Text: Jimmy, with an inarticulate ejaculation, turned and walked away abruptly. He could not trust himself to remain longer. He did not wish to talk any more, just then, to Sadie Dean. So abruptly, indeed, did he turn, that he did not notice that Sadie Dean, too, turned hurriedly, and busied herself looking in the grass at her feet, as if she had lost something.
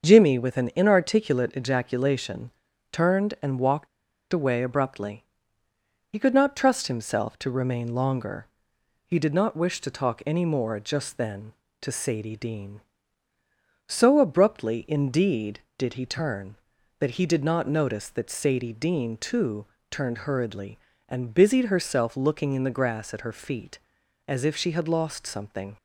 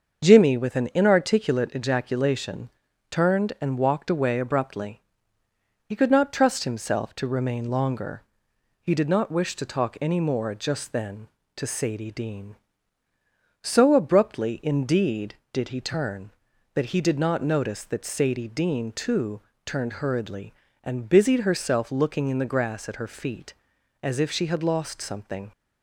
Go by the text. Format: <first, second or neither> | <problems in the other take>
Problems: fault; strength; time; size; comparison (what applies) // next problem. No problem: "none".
second | starts louder than the rest; until 1.1 s; 6.5 dB; also in the second // pauses between "walked" and "away"; at 3.8 s; 0.44 s long